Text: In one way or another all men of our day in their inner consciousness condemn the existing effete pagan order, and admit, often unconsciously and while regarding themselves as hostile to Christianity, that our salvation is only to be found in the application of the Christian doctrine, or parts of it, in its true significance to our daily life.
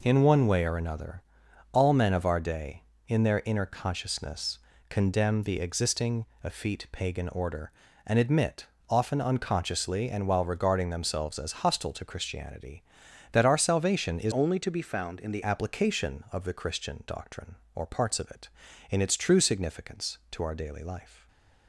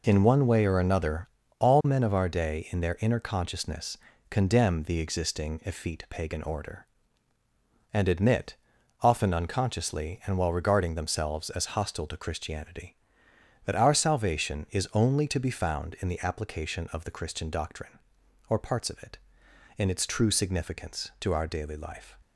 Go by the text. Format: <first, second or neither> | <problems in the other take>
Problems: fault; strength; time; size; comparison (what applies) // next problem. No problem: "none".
second | pauses between "another" and "all"; noticeable; at 1.2 s; 0.52 s long; slight in the second // pauses between "consciousness" and "condemn"; slight; at 4.5 s; 0.32 s long; slight in the second // pauses between "existing" and "effete"; slight; at 6.2 s; 0.18 s long // changes voice from "only" to "the"; from 14.3 to 15.4 s; 1.1 s long // stays silent after the last word; slight; from 21.0 s on; 0.6 s long